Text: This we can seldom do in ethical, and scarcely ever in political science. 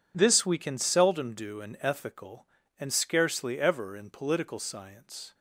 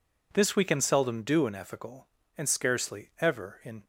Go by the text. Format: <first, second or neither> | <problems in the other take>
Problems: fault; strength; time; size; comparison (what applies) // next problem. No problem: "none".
first | stops before "political science"; at 3.8 s